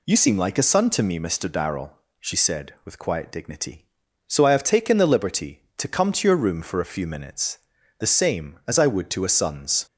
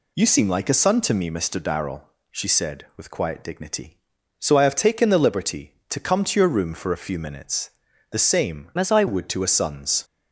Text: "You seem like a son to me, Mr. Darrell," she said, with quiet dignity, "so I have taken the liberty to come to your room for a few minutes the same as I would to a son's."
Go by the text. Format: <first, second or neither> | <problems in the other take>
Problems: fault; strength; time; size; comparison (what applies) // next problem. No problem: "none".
first | pauses between "minutes" and "the"; at 7.6 s; 0.40 s long; also in the first // changes voice from "as" to "I"; from 8.7 to 9.0 s; 0.3 s long